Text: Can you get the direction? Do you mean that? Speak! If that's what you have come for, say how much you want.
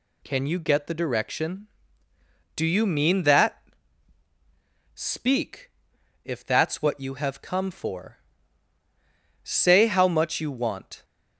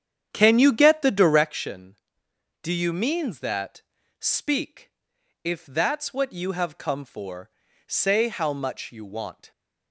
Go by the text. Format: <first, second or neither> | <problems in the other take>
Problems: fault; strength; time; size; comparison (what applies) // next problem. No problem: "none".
first | starts louder than the rest; strong; until 1.5 s; 8.5 dB